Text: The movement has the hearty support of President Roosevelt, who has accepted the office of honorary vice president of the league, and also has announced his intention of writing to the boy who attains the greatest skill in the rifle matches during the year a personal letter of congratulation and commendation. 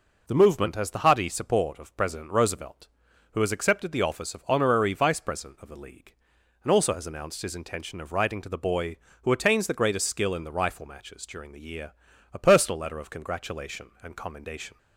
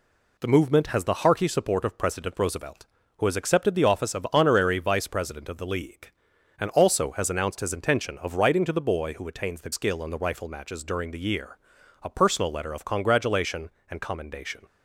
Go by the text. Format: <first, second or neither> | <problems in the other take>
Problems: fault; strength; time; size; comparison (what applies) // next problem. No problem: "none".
first | skips "greatest"; at 9.7 s // pauses between "year" and "a"; noticeable; at 11.5 s; 0.46 s long; also in the first